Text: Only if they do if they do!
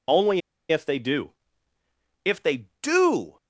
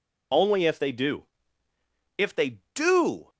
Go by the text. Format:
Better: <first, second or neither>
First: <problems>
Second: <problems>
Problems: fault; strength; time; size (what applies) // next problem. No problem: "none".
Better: second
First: pauses between "Only" and "if"; slight; at 0.4 s; 0.30 s long // pauses between "do" and "if"; noticeable; at 1.3 s; 0.92 s long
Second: pauses between "do" and "if"; noticeable; at 1.2 s; 0.92 s long